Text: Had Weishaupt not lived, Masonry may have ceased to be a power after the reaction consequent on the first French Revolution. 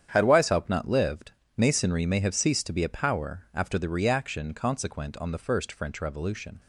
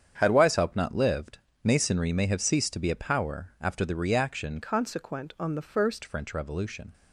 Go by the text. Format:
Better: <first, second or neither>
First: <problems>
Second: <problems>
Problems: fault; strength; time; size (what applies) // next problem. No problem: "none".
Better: first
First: starts louder than the rest; strong; until 1.1 s; 9 dB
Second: starts louder than the rest; strong; until 1.1 s; 8 dB // changes voice from "consequent" to "first"; from 4.6 to 6.0 s; 1.4 s long